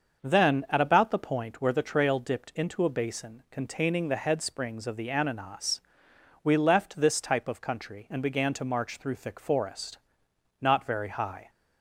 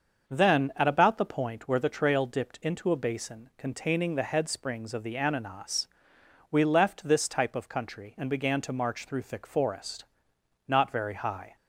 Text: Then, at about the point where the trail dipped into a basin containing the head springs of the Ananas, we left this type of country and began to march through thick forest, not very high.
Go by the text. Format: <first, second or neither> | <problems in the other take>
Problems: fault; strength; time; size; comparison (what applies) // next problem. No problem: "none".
neither | starts louder than the rest; the same in both